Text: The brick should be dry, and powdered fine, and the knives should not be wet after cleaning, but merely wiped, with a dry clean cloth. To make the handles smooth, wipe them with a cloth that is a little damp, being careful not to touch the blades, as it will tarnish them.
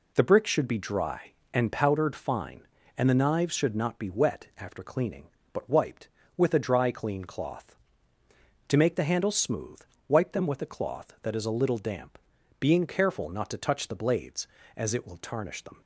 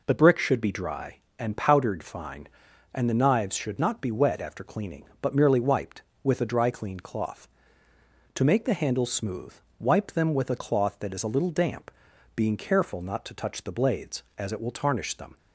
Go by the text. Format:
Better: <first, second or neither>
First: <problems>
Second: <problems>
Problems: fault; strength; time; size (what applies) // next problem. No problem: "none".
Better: second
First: skips "merely"; at 5.6 s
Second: none